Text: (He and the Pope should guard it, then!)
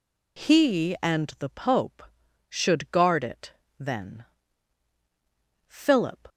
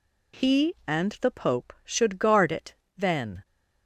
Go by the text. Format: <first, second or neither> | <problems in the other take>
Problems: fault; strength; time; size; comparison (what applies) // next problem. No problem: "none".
second | goes on to say "Philip"; noticeable; from 5.6 s on; 0.62 s long